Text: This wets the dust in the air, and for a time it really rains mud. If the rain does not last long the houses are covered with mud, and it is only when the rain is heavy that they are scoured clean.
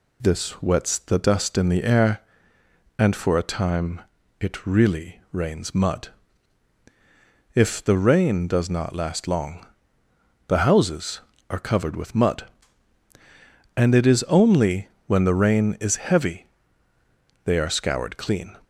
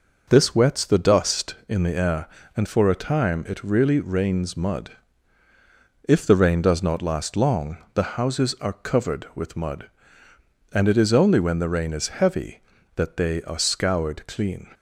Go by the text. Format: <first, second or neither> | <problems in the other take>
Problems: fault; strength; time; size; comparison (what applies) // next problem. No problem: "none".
second | pauses between "time" and "it"; at 4.0 s; 0.38 s long // pauses between "long" and "the"; noticeable; at 9.6 s; 0.82 s long; slight in the second // pauses between "only" and "when"; slight; at 14.8 s; 0.18 s long // skips "that"; at 16.9 s